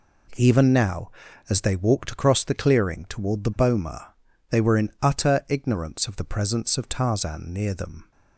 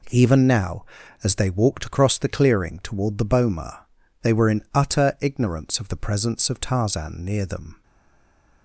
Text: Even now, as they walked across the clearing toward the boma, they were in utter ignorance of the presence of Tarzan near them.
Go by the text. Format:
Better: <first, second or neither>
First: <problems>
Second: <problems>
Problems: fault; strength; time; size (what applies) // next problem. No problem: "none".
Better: first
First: none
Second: stays silent after the last word; slight; from 7.8 s on; 0.8 s long